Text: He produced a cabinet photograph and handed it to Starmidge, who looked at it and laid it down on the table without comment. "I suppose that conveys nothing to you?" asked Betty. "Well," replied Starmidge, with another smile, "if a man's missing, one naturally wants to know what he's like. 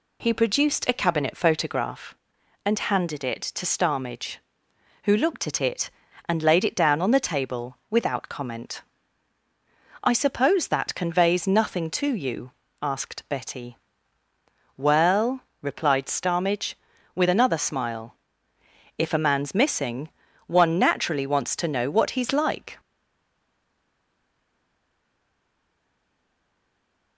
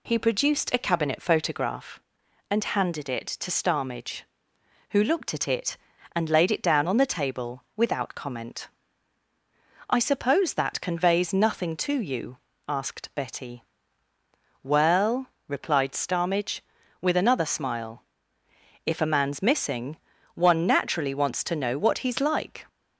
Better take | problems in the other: second | stays silent after the last word; strong; from 22.7 s on; 4.4 s long

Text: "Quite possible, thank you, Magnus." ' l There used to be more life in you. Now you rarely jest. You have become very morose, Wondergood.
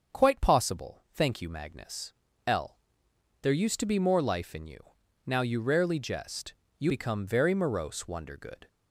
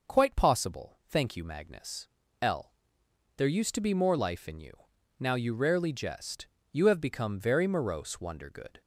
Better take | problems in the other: second | pauses between "l" and "There"; noticeable; at 2.7 s; 0.62 s long; noticeable in the second // skips "have"; at 6.8 s

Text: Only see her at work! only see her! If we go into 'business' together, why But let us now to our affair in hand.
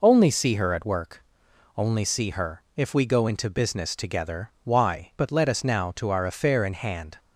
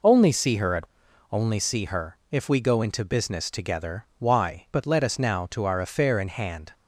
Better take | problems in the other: first | skips "work"; at 1.0 s

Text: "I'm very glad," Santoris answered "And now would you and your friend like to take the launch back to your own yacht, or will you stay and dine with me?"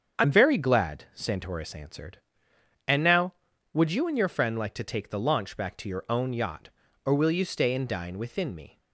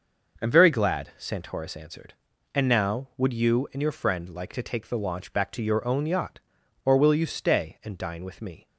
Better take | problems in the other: second | starts louder than the rest; strong; until 1.2 s; 7.5 dB // says "within" for "with"; at 8.1 s

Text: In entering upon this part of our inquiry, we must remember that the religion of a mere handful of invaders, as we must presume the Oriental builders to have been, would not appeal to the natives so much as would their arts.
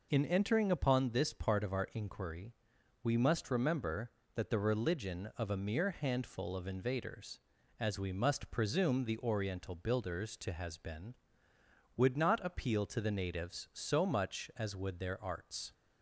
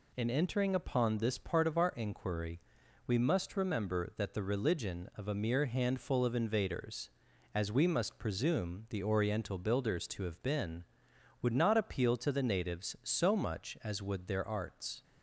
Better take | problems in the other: second | says "has" for "have"; at 10.5 s

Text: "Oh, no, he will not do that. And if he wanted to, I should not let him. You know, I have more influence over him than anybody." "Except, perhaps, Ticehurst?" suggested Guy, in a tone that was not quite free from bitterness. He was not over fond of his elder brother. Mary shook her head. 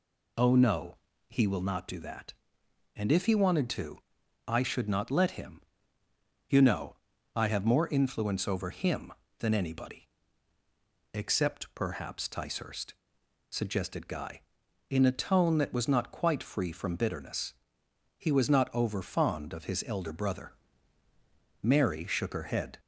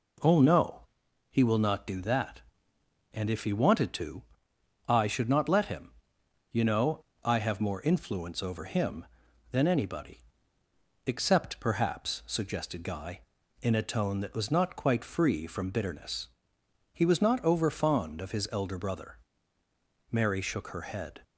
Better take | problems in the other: first | skips "Ticehurst"; at 12.2 s

